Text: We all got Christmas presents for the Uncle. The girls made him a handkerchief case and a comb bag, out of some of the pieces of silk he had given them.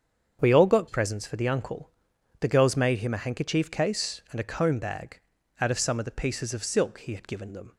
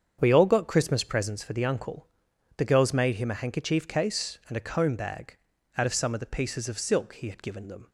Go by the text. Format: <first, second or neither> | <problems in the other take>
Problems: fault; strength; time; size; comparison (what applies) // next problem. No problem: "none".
second | starts louder than the rest; strong; until 1.4 s; 7.5 dB; strong in the second // skips "Christmas"; at 0.8 s